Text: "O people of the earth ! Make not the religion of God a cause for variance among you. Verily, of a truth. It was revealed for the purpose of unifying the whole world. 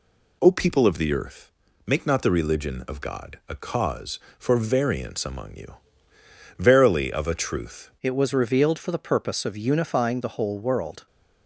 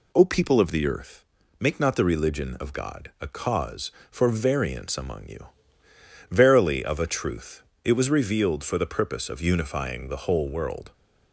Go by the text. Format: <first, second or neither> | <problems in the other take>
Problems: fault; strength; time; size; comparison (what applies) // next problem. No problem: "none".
second | changes voice at "It"; from 8.0 s on; 3.0 s long